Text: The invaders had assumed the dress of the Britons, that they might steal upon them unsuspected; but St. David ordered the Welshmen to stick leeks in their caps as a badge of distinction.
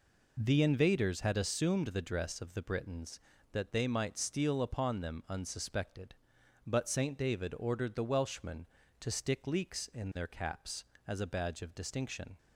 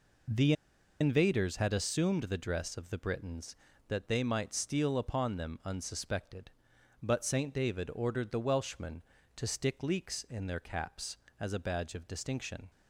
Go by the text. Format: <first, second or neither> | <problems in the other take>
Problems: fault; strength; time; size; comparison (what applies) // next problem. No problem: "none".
first | pauses between "The" and "invaders"; noticeable; at 0.5 s; 0.47 s long